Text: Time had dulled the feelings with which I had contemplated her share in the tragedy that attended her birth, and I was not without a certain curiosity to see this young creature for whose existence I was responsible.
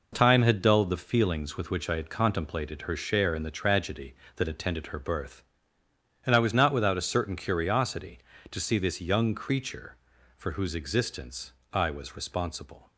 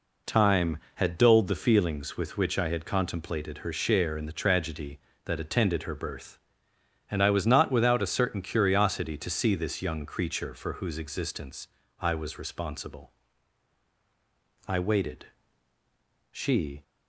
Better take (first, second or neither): first